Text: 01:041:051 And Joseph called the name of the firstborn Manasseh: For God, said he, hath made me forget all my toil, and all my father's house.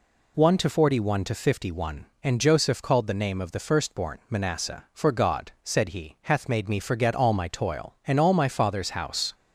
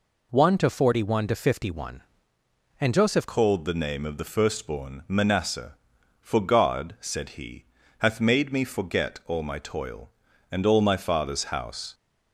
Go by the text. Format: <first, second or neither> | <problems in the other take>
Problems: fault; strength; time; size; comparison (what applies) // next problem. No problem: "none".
first | changes voice at "called"; from 3.2 s on; 8.7 s long